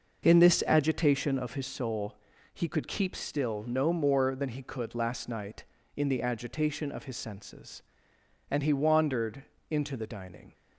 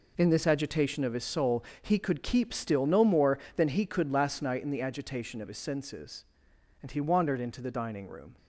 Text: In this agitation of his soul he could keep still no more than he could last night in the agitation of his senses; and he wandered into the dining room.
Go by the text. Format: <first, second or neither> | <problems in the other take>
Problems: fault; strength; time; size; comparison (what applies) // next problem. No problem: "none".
second | pauses between "soul" and "he"; at 2.1 s; 0.40 s long; slight in the second // pauses between "wandered" and "into"; slight; at 9.4 s; 0.26 s long // stops before "room"; at 10.5 s